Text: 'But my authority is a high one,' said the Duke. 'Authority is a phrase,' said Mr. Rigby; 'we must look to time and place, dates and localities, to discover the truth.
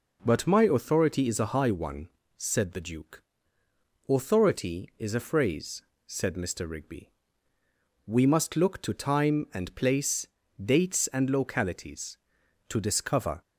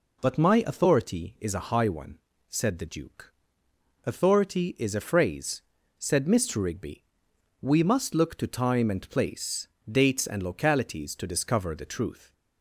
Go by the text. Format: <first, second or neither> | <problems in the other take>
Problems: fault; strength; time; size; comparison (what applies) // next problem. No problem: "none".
second | stops before "the truth"; at 13.4 s